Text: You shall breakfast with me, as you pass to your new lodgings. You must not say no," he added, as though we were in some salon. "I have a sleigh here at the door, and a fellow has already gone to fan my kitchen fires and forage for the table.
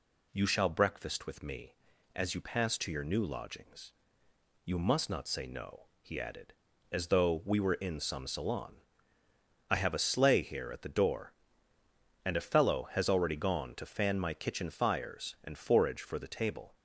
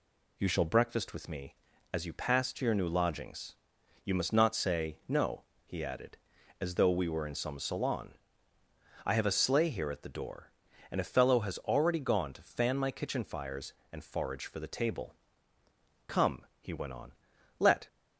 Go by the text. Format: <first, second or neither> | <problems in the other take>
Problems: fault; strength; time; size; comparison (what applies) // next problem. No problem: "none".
first | goes on to say "Come he went on let"; strong; from 16.0 s on; 1.8 s long